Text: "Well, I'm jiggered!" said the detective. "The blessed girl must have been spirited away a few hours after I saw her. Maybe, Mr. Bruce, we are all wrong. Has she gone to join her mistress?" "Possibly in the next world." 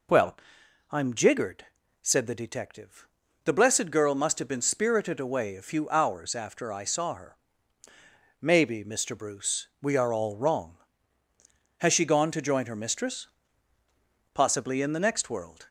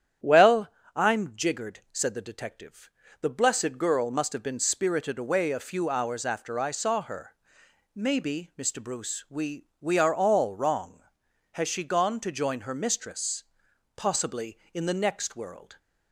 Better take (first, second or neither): first